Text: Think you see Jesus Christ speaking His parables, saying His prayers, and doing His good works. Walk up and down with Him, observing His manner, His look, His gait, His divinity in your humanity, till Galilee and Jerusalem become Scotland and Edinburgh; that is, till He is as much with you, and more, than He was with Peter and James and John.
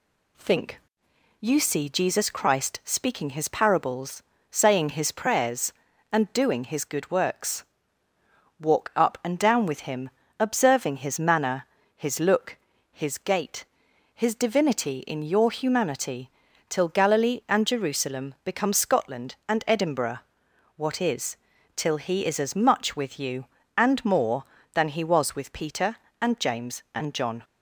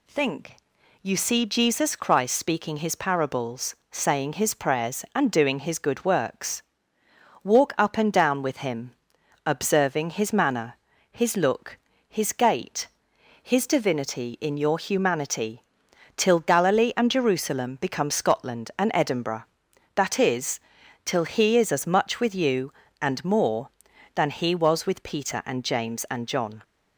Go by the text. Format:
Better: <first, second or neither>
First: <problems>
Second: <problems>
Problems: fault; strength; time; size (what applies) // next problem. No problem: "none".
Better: second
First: pauses between "Think" and "you"; noticeable; at 0.7 s; 0.60 s long // says "what" for "that"; at 20.7 s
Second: pauses between "Think" and "you"; noticeable; at 0.5 s; 0.46 s long